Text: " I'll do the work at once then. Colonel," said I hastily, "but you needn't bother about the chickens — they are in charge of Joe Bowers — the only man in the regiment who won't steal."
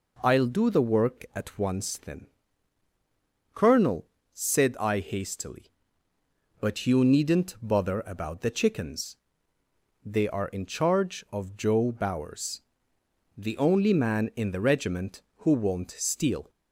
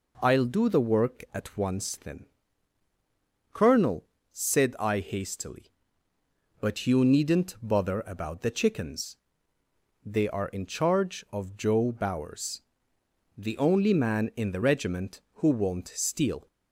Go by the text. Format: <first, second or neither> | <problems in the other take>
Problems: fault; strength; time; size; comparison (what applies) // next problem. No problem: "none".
neither | none